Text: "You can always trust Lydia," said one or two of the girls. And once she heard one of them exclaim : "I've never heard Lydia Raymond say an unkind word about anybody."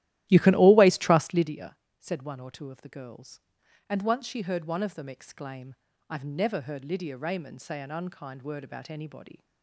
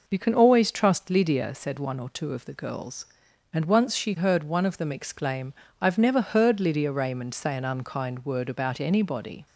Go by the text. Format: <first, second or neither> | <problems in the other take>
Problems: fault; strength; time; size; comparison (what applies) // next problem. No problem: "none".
second | starts louder than the rest; strong; until 1.5 s; 14 dB